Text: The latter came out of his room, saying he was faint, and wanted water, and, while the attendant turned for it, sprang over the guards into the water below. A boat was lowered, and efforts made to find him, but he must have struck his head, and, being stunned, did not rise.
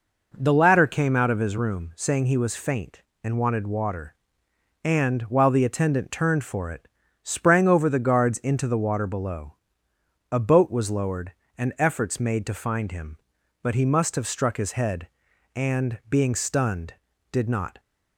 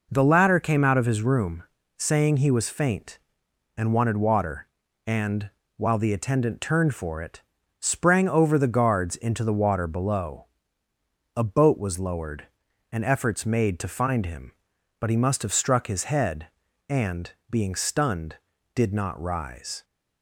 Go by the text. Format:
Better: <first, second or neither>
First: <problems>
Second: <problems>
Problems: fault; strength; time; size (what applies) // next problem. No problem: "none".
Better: second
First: stops before "rise"; at 17.7 s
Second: none